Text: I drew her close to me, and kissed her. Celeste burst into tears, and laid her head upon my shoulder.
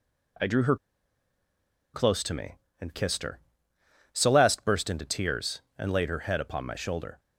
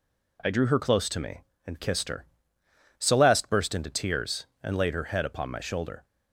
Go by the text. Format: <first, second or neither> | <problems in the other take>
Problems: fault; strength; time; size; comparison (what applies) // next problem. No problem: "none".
second | pauses between "her" and "close"; at 0.7 s; 1.1 s long